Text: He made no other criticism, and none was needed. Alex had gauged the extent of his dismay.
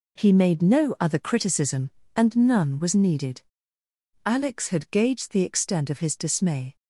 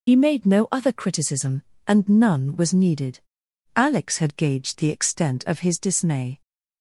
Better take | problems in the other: first | loses the start of "He"; at 0.0 s; 65 ms

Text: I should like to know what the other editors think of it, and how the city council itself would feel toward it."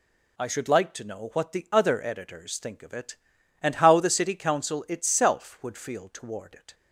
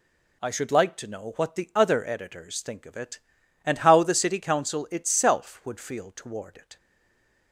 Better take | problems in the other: first | stays silent after the last word; slight; from 6.7 s on; 0.8 s long

